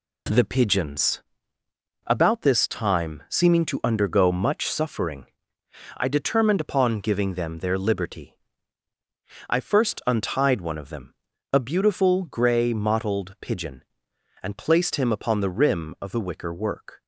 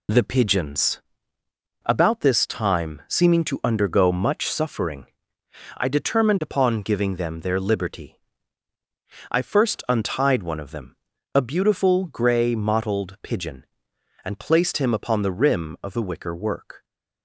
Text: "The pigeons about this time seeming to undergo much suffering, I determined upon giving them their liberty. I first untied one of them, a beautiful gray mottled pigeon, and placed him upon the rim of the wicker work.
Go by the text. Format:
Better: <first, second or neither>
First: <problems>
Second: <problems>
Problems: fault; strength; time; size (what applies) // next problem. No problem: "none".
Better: first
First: pauses between "pigeons" and "about"; noticeable; at 1.2 s; 0.84 s long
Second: loses the start of "The"; at 0.0 s; 40 ms // pauses between "pigeons" and "about"; noticeable; at 1.0 s; 0.84 s long